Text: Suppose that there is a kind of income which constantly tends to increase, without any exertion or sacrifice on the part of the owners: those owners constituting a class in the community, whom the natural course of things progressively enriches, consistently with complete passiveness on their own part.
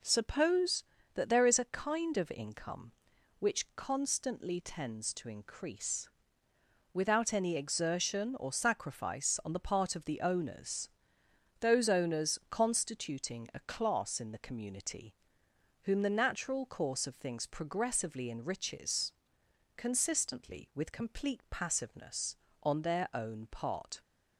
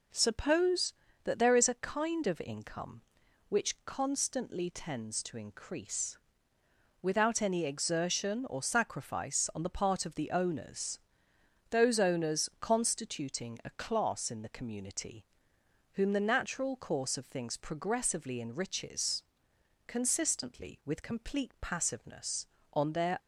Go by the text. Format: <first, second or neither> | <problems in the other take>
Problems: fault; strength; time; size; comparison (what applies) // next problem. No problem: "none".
first | stops before "own part"; at 23.1 s